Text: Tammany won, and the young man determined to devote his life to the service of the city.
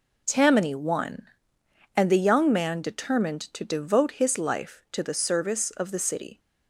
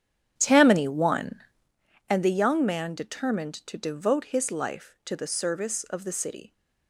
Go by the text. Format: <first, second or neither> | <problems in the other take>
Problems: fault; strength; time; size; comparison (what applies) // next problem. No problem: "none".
first | starts louder than the rest; strong; until 1.7 s; 10 dB